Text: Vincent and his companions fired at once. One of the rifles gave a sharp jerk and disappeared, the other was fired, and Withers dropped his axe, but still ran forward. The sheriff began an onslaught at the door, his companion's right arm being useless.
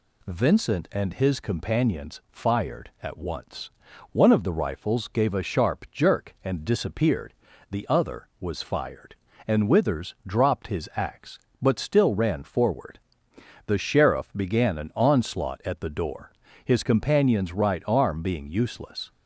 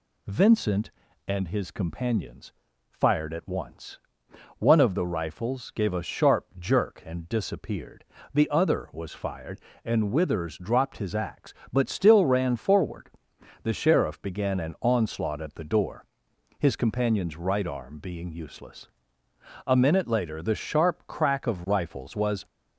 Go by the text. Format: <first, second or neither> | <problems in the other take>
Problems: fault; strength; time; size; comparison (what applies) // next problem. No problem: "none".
first | pauses between "companions" and "fired"; at 2.5 s; 0.40 s long // goes on to say "A minute later the sharp crack of rifles was"; strong; from 19.6 s on; 2.7 s long